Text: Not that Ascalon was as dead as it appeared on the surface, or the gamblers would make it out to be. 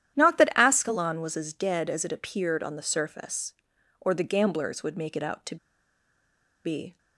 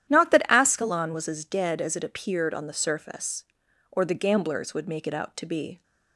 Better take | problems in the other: second | starts louder than the rest; strong; until 1.2 s; 11 dB; strong in the second // pauses between "to" and "be"; at 5.5 s; 1.0 s long

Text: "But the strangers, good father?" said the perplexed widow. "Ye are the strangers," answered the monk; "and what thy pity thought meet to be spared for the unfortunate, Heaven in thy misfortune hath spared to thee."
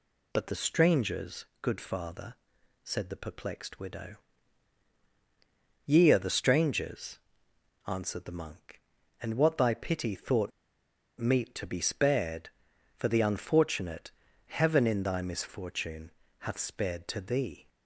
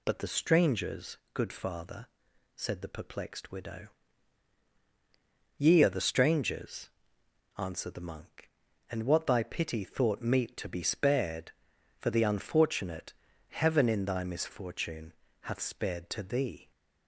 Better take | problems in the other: second | pauses between "thought" and "meet"; noticeable; at 10.5 s; 0.69 s long // pauses between "misfortune" and "hath"; slight; at 16.1 s; 0.28 s long; slight in the second

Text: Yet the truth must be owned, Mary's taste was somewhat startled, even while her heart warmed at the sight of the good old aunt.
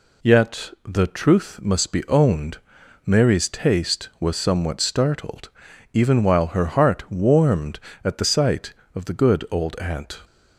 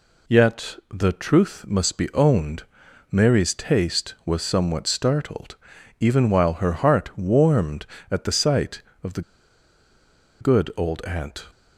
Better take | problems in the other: first | pauses between "the" and "good"; at 9.2 s; 1.1 s long

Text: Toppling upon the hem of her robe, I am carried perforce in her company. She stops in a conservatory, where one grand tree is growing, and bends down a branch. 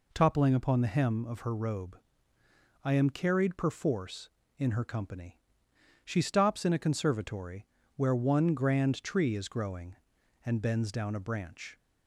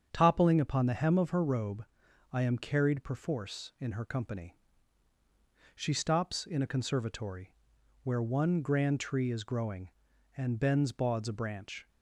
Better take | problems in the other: first | starts louder than the rest; strong; until 1.1 s; 7.5 dB // says "bauds" for "down"; at 10.9 s

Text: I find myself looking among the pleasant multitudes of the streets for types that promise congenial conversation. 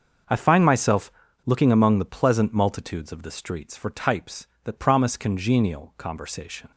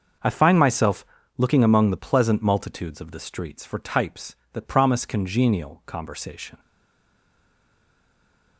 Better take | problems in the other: first | starts louder than the rest; until 1.5 s; 6.5 dB; also in the first // pauses between "myself" and "looking"; slight; at 1.0 s; 0.32 s long; slight in the first // stays silent after the last word; noticeable; from 6.5 s on; 2.0 s long

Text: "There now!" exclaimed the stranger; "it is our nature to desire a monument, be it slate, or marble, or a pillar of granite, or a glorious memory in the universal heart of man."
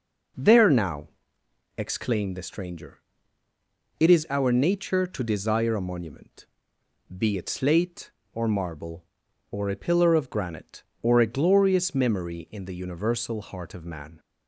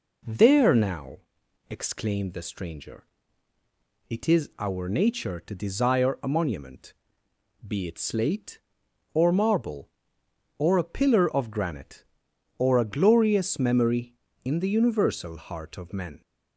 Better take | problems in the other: first | says "men" for "man"; at 15.9 s

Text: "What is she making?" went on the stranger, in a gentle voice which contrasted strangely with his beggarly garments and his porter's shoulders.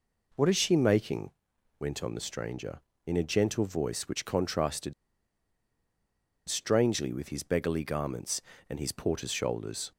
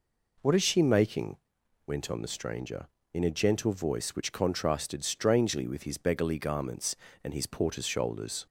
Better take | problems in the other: second | pauses between "contrasted" and "strangely"; strong; at 4.9 s; 1.5 s long

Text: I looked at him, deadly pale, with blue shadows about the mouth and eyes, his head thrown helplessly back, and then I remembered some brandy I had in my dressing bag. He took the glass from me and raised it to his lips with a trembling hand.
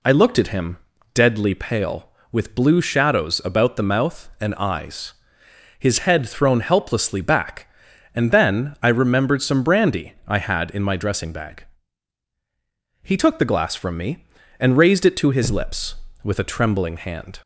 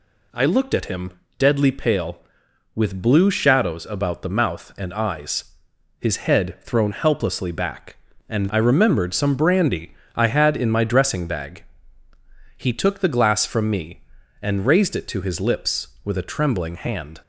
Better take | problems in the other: first | skips "then"; at 8.4 s // pauses between "brandy" and "I"; slight; at 9.9 s; 0.22 s long

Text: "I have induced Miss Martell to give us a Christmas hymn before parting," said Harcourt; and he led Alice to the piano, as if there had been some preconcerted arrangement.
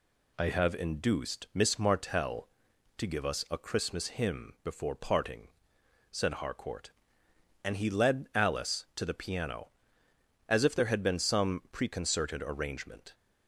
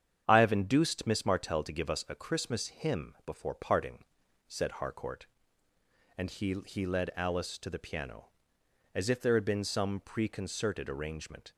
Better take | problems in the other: first | starts louder than the rest; strong; until 1.2 s; 8.5 dB // says "he" twice; at 6.6 s

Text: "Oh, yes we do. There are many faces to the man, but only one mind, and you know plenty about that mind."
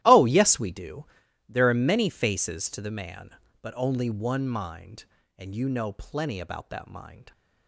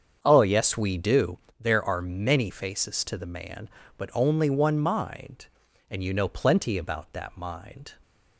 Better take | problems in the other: second | gets quieter; strong; throughout; 16 dB // starts louder than the rest; strong; until 1.0 s; 14 dB; strong in the second

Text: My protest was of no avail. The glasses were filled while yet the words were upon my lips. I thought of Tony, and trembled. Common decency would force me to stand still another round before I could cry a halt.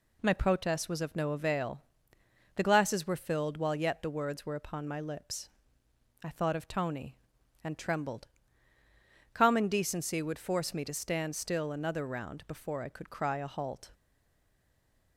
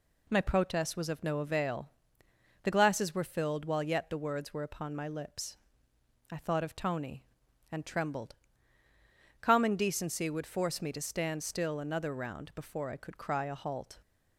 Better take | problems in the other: second | stays silent after the last word; noticeable; from 13.9 s on; 1.2 s long

